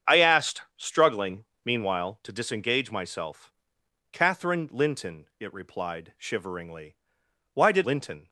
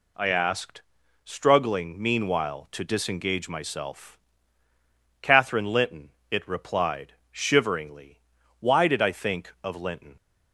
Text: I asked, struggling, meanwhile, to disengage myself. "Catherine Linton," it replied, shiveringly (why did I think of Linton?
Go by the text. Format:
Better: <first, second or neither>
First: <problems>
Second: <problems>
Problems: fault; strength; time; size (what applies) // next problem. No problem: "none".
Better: second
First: starts louder than the rest; strong; until 1.2 s; 7.5 dB // skips "I think of"; at 7.8 s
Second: none